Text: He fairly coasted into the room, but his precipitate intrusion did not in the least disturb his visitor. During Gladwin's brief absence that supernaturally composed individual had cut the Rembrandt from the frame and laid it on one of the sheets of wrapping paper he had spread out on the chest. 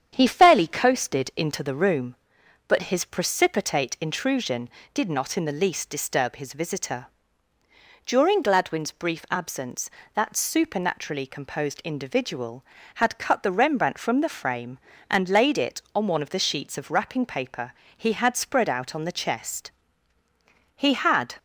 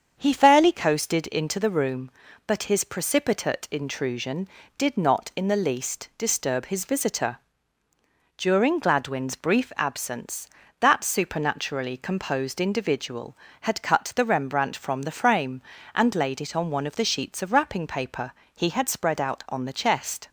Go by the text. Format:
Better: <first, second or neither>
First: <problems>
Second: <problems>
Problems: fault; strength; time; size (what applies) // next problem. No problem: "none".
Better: second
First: starts louder than the rest; strong; until 1.1 s; 8.5 dB // pauses between "paper" and "he"; slight; at 17.7 s; 0.26 s long // goes on to say "He had"; from 20.7 s on; 0.60 s long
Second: starts louder than the rest; strong; until 1.1 s; 7.5 dB // pauses between "paper" and "he"; slight; at 18.3 s; 0.22 s long